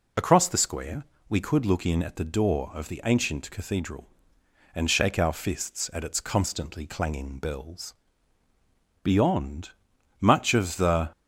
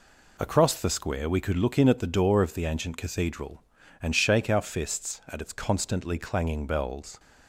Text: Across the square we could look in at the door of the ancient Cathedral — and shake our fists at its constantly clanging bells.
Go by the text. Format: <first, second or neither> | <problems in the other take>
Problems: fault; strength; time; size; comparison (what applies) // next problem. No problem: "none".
second | pauses between "square" and "we"; slight; at 1.0 s; 0.26 s long // goes on to say "Beyond much of the"; strong; from 9.0 s on; 2.0 s long